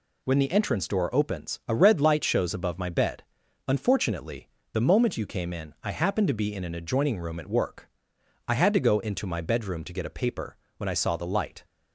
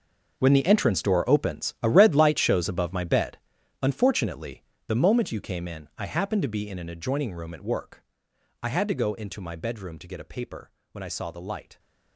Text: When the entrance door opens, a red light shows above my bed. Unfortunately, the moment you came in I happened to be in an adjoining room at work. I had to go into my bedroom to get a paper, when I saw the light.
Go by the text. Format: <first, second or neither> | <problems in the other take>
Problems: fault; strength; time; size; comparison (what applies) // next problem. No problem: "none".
first | gets quieter; strong; throughout; 15.5 dB